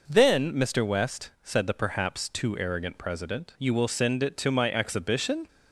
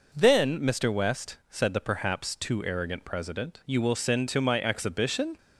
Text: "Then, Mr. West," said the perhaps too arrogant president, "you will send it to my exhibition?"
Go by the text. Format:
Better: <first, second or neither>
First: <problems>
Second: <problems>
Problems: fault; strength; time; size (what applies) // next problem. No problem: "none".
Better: first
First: none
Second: skips "it"; at 4.2 s